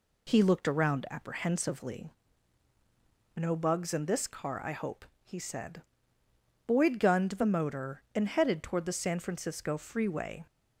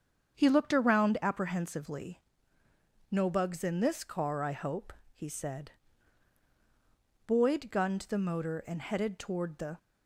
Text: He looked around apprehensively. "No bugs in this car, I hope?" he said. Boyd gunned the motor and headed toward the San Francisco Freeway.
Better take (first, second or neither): first